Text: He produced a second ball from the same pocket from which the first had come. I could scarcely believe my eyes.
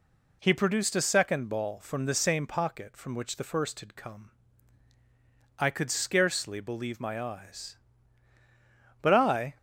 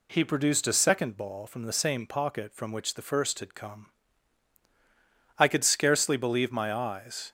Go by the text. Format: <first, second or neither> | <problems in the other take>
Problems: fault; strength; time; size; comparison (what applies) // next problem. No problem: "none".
second | goes on to say "But I"; from 9.0 s on; 0.56 s long